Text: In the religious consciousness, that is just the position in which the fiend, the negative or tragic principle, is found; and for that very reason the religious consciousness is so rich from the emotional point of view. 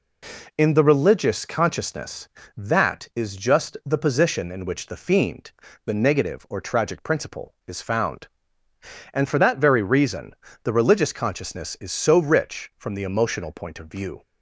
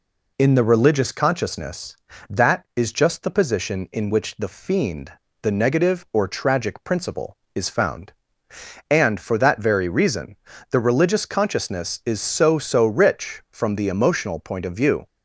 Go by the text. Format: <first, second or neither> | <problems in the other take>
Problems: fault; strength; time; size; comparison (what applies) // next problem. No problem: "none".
first | pauses between "reason" and "the"; at 10.3 s; 0.38 s long; slight in the first // says "so" twice; at 12.5 s